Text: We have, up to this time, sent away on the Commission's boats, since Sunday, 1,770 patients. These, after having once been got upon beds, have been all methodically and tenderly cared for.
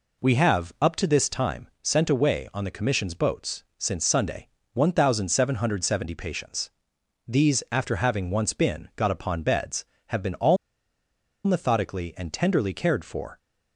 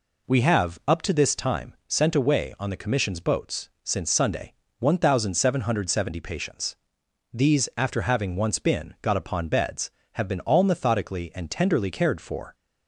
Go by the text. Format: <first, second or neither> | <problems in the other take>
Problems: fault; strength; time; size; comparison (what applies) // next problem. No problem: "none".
second | pauses between "all" and "methodically"; noticeable; at 10.5 s; 0.89 s long